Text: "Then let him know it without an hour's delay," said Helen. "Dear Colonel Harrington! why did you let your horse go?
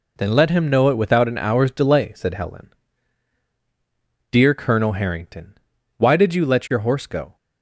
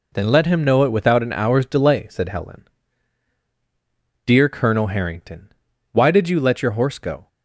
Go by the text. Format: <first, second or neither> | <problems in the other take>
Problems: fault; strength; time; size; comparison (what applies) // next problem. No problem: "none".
neither | none